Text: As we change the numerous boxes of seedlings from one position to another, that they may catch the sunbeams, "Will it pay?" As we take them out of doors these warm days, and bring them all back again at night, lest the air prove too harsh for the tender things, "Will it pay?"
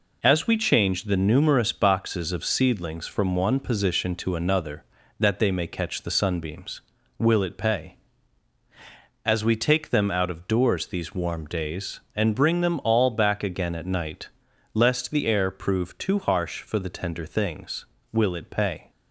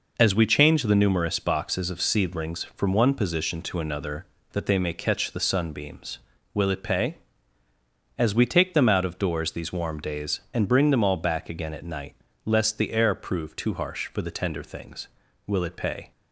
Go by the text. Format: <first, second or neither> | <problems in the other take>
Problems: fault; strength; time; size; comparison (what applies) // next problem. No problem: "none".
neither | none